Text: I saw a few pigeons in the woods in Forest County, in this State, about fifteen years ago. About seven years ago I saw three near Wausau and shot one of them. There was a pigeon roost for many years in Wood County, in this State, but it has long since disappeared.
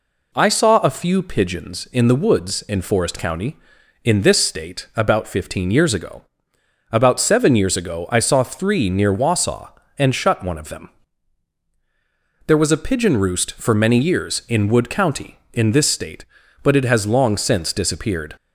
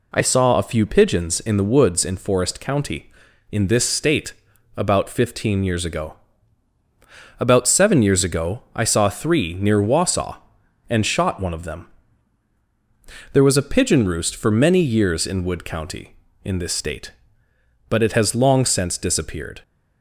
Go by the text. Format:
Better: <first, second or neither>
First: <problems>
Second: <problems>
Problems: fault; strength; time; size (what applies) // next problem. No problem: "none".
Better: second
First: says "shut" for "shot"; at 10.1 s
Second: none